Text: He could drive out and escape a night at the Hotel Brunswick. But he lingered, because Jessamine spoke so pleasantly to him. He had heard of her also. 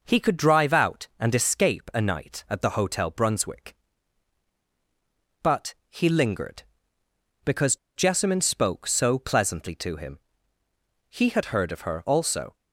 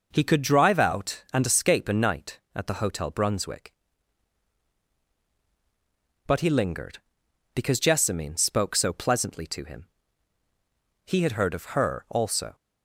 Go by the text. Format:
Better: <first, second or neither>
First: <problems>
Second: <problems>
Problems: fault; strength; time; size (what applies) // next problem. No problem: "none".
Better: second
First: pauses between "because" and "Jessamine"; slight; at 7.7 s; 0.20 s long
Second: none